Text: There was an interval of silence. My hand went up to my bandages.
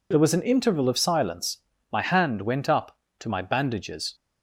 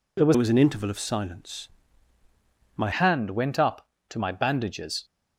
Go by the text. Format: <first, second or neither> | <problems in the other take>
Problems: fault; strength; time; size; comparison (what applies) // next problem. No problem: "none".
first | changes voice from "was" to "My"; from 0.3 to 2.9 s; 2.6 s long